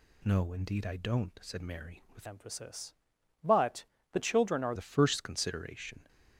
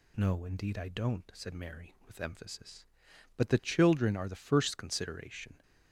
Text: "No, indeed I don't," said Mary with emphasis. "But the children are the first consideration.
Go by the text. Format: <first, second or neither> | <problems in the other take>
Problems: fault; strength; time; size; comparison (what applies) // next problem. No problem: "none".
second | changes voice from "emphasis" to "are"; from 2.2 to 4.7 s; 2.5 s long // pauses between "But" and "the"; slight; at 3.8 s; 0.26 s long